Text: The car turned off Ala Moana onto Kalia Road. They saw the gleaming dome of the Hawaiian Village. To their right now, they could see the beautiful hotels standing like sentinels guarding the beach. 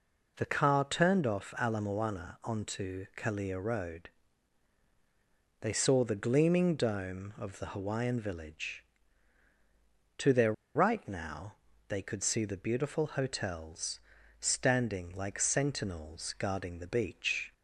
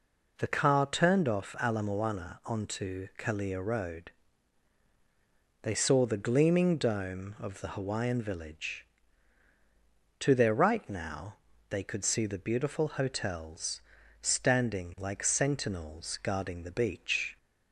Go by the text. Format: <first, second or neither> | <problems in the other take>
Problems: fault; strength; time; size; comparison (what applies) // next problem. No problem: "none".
second | pauses between "their" and "right"; slight; at 10.5 s; 0.23 s long // pauses between "hotels" and "standing"; at 13.9 s; 0.40 s long; also in the second